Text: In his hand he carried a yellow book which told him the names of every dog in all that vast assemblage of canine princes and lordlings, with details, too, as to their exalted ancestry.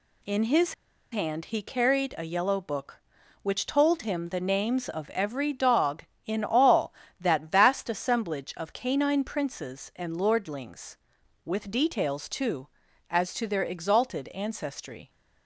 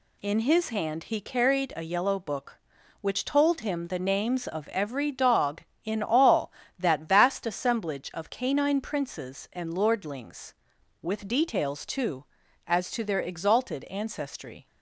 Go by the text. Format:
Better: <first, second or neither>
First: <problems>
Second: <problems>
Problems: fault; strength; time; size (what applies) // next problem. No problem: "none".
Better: second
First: pauses between "his" and "hand"; at 0.7 s; 0.37 s long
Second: none